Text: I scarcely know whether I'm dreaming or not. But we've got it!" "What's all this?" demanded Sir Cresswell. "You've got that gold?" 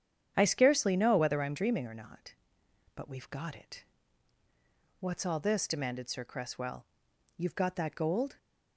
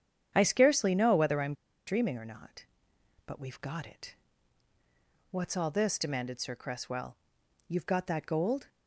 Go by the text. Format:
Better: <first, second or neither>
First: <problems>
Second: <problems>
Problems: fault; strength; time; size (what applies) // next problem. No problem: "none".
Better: first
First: starts louder than the rest; strong; until 1.3 s; 8.5 dB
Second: starts louder than the rest; strong; until 1.3 s; 8.5 dB // pauses between "I'm" and "dreaming"; slight; at 1.5 s; 0.33 s long